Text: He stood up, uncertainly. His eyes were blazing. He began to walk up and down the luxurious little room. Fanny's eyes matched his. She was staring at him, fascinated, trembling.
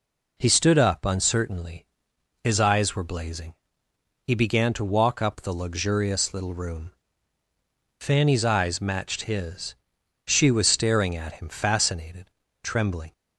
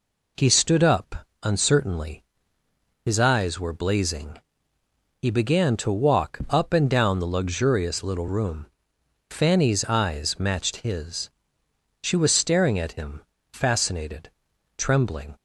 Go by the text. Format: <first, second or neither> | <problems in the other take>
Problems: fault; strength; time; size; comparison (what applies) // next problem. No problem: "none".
second | skips "and down"; at 5.3 s